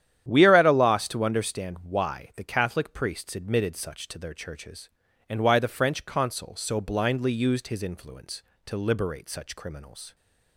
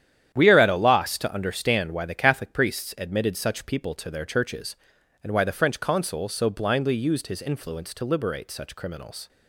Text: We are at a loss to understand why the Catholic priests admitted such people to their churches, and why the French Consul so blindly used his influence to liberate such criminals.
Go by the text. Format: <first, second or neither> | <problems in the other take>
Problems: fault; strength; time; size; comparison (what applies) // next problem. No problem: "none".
second | starts louder than the rest; strong; until 1.3 s; 10 dB; strong in the second // skips "people"; at 4.0 s